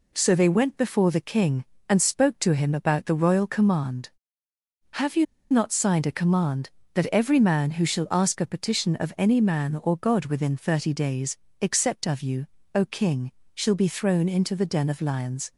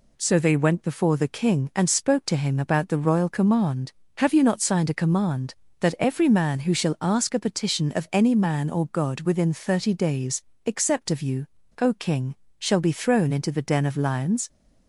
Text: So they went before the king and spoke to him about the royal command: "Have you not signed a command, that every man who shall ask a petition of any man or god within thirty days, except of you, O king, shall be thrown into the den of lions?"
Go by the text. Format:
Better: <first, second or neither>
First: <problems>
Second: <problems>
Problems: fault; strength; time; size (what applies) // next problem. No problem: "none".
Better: second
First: pauses between "you" and "not"; slight; at 5.2 s; 0.26 s long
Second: none